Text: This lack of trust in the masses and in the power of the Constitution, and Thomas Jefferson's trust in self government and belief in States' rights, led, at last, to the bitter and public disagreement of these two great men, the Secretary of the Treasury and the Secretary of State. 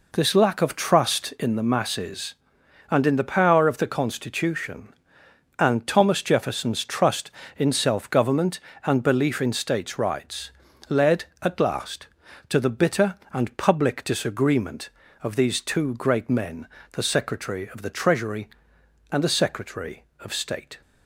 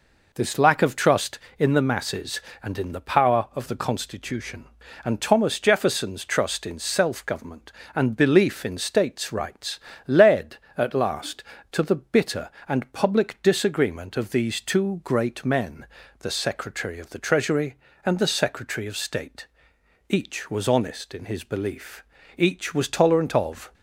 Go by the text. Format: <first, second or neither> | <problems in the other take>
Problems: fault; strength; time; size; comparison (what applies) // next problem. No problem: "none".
first | goes on to say "Each was honest in his belief each was tolerant of"; strong; from 20.0 s on; 3.6 s long